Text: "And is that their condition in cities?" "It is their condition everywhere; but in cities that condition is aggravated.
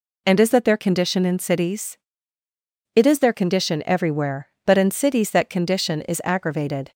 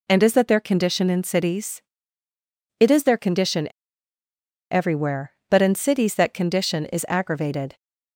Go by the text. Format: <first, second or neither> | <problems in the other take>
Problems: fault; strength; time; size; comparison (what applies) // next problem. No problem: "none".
first | pauses between "condition" and "everywhere"; at 3.6 s; 1.0 s long